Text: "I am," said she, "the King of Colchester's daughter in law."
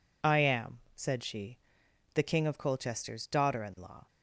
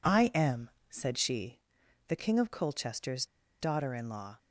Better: first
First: none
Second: pauses between "Colchester's" and "daughter"; at 3.2 s; 0.36 s long

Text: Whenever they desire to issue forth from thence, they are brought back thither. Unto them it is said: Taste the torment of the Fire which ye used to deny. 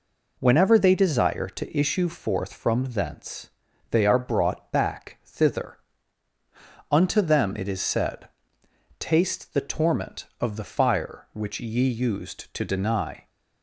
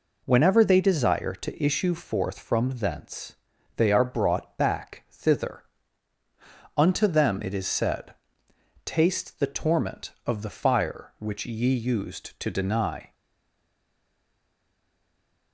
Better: first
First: none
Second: stays silent after the last word; from 13.1 s on; 2.4 s long

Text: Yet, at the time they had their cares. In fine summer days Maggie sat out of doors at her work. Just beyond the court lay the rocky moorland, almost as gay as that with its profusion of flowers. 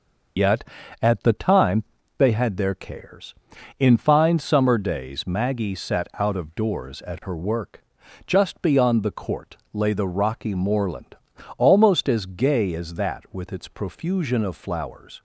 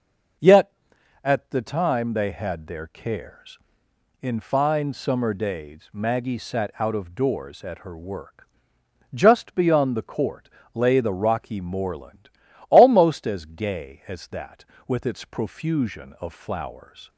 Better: second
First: loses the start of "Yet"; at 0.3 s; 75 ms // pauses between "time" and "they"; slight; at 1.8 s; 0.34 s long // pauses between "court" and "lay"; slight; at 9.5 s; 0.18 s long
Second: pauses between "court" and "lay"; slight; at 10.4 s; 0.26 s long

